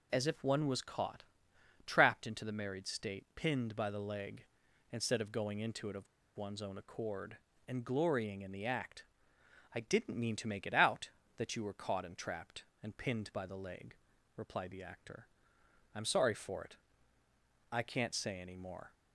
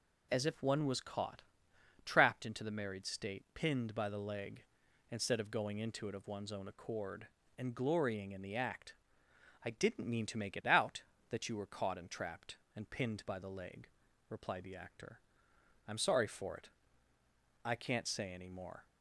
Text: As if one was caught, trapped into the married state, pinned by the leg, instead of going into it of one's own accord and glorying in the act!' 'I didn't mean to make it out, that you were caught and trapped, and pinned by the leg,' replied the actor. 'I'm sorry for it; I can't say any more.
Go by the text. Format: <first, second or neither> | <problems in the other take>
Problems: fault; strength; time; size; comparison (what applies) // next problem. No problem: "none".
second | pauses between "of" and "one's"; slight; at 6.0 s; 0.30 s long